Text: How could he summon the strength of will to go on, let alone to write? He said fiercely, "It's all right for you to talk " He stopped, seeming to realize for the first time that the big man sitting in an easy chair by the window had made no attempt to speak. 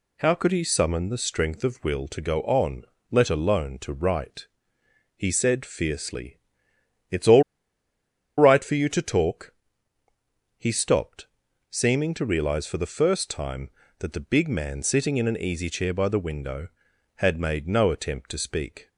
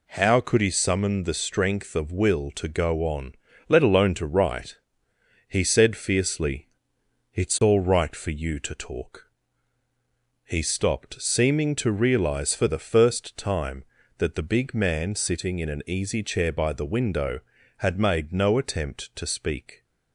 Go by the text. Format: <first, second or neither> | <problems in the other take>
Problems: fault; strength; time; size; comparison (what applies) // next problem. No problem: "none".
second | pauses between "all" and "right"; noticeable; at 7.4 s; 0.95 s long